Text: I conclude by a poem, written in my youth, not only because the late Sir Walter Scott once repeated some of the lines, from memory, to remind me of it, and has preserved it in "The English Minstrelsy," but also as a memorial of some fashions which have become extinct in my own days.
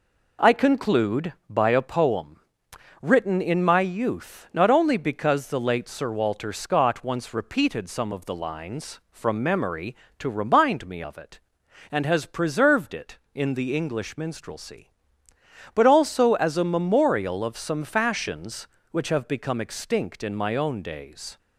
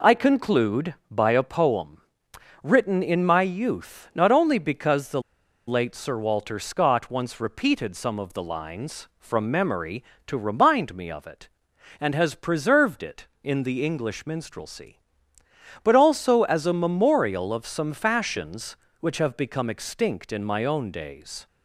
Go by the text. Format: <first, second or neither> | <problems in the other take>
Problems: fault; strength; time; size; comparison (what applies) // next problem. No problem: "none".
first | pauses between "the" and "late"; noticeable; at 5.2 s; 0.46 s long